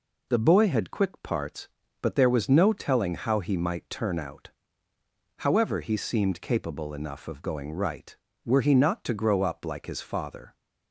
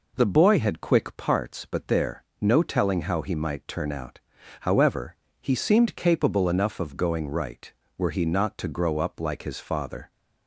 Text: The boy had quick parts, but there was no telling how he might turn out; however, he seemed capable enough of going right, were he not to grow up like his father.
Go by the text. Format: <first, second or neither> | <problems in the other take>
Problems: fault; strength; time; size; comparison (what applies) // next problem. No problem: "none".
first | skips "was"; at 2.3 s